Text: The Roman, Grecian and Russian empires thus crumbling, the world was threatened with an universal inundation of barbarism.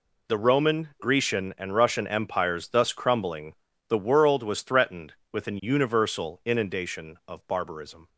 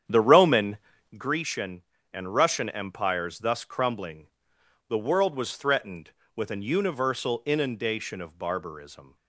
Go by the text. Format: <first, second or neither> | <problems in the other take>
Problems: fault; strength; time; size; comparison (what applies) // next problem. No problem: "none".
first | starts louder than the rest; strong; until 1.3 s; 8.5 dB